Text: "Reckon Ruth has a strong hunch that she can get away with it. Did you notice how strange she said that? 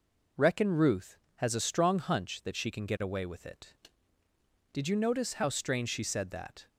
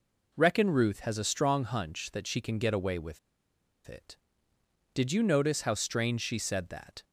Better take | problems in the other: first | pauses between "with" and "it"; noticeable; at 3.1 s; 0.68 s long

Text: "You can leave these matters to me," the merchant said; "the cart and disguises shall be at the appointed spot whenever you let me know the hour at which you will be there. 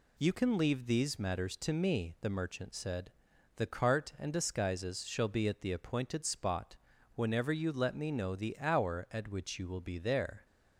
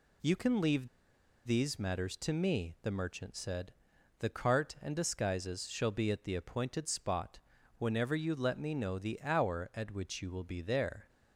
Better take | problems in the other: first | pauses between "leave" and "these"; noticeable; at 0.8 s; 0.58 s long // pauses between "spot" and "whenever"; at 7.3 s; 0.40 s long; also in the first

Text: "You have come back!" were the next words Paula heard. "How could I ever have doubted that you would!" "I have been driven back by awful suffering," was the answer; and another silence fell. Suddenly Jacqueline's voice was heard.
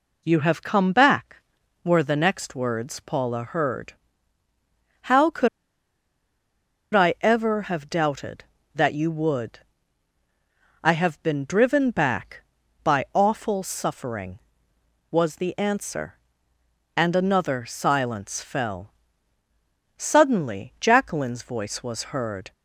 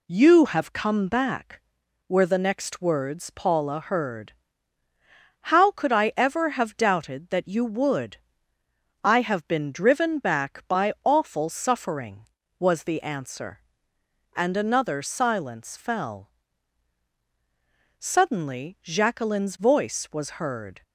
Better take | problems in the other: second | pauses between "could" and "I"; strong; at 5.4 s; 1.4 s long

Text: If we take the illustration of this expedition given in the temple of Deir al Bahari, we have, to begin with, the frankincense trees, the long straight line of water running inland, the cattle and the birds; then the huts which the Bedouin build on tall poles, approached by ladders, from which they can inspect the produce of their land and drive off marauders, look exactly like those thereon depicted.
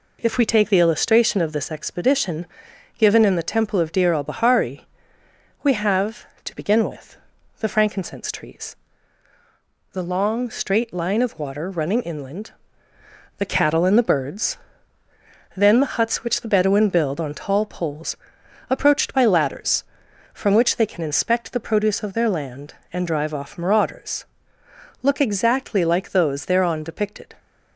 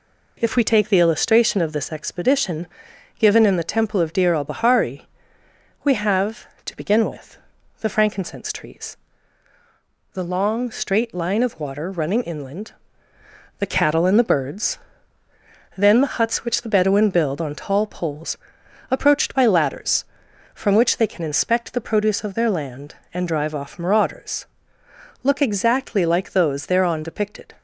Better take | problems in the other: neither | pauses between "expedition" and "given"; noticeable; the same in both

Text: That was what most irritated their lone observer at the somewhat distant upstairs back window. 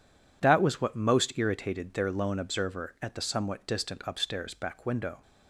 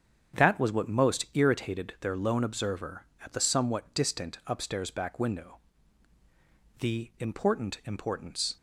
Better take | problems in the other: first | starts louder than the rest; strong; until 1.4 s; 8 dB // goes on to say "The important importance"; strong; from 6.8 s on; 1.7 s long

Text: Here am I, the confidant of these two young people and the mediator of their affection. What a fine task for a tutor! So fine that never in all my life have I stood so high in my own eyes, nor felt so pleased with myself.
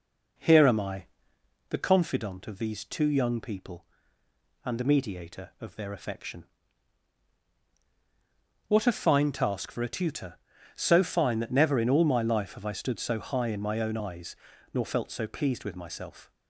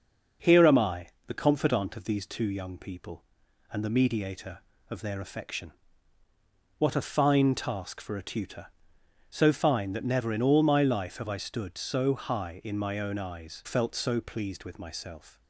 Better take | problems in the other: first | skips "nor"; at 13.6 s

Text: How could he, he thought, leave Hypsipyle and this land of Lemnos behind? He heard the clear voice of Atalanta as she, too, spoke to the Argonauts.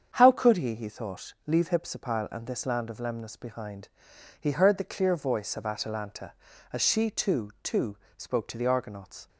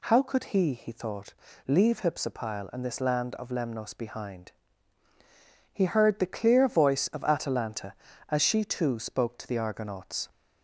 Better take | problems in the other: second | starts louder than the rest; strong; until 1.1 s; 7.5 dB // says "too" twice; at 7.6 s

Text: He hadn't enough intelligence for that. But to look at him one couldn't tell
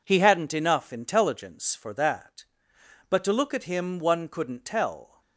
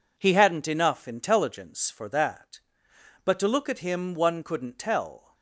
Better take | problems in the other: neither | none

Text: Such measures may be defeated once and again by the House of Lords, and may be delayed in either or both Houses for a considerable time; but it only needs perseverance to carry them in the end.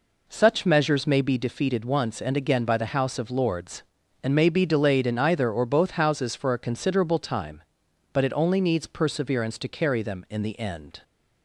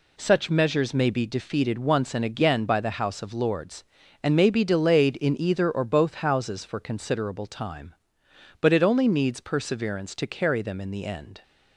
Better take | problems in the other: first | skips "a"; at 6.8 s

